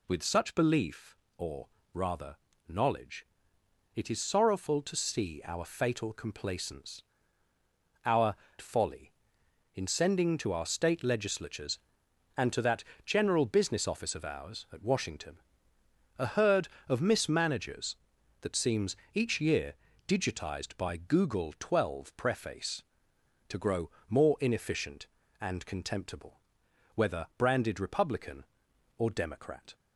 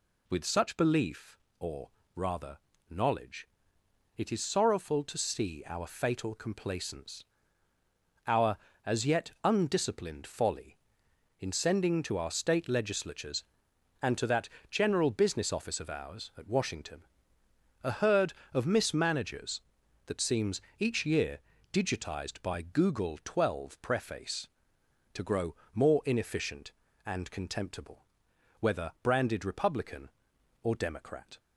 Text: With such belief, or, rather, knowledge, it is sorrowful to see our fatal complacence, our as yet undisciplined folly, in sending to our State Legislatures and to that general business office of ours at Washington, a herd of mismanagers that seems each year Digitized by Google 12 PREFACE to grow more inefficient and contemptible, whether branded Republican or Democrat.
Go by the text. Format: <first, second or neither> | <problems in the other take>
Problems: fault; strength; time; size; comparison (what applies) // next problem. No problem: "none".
second | skips "as yet undisciplined"; at 8.4 s // pauses between "that" and "general"; slight; at 12.8 s; 0.24 s long; slight in the second // pauses between "seems" and "each"; slight; at 18.9 s; 0.18 s long; slight in the second // pauses between "year" and "Digitized"; slight; at 19.7 s; 0.34 s long; slight in the second // pauses between "grow" and "more"; slight; at 23.8 s; 0.20 s long; slight in the second